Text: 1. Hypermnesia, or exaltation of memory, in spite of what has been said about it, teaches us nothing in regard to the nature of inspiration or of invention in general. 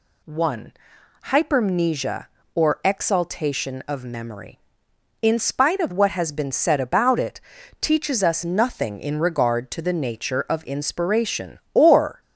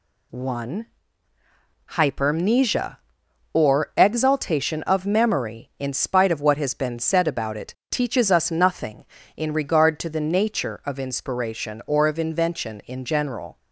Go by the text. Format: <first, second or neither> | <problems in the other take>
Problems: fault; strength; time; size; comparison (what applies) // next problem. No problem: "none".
second | stops before "of invention in general"; at 12.2 s